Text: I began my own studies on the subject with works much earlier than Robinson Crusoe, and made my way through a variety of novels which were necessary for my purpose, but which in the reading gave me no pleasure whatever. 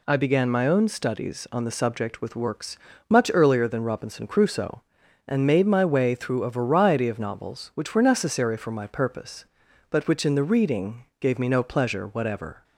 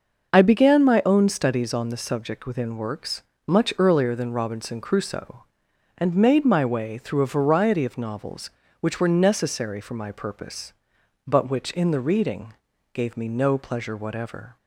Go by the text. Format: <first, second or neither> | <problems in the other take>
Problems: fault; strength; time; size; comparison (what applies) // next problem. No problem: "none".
first | starts louder than the rest; noticeable; until 1.3 s; 6 dB // says "within" for "with"; at 2.4 s // pauses between "works" and "much"; slight; at 3.2 s; 0.24 s long; slight in the first // pauses between "reading" and "gave"; at 12.5 s; 0.38 s long; slight in the first